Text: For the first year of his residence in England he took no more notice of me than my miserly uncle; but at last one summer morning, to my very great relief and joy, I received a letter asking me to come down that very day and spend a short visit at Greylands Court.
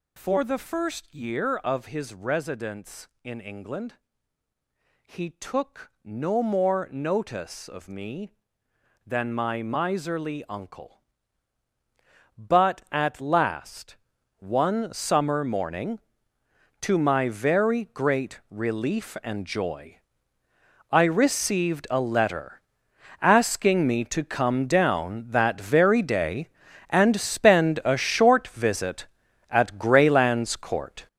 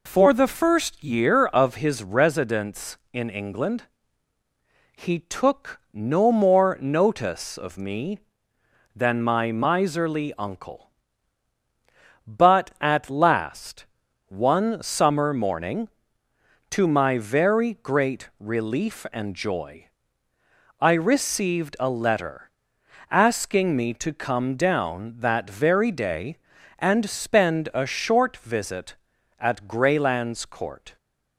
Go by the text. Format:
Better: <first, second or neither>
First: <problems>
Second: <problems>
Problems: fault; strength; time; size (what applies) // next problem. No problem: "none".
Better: second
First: gets louder; strong; throughout; 10 dB // pauses between "England" and "he"; at 3.9 s; 1.1 s long // pauses between "last" and "one"; at 13.9 s; 0.44 s long // pauses between "letter" and "asking"; noticeable; at 22.5 s; 0.62 s long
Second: pauses between "England" and "he"; at 3.8 s; 1.1 s long // pauses between "last" and "one"; at 13.8 s; 0.44 s long // pauses between "letter" and "asking"; noticeable; at 22.4 s; 0.62 s long